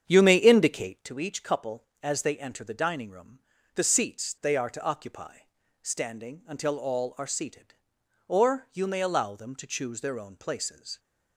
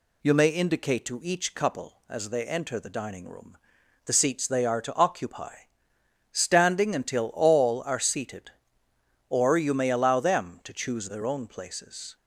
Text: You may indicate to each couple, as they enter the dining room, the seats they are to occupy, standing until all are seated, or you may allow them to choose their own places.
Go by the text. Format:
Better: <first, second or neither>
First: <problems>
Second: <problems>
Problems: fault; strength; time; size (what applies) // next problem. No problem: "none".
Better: second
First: starts louder than the rest; strong; until 1.1 s; 8 dB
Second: none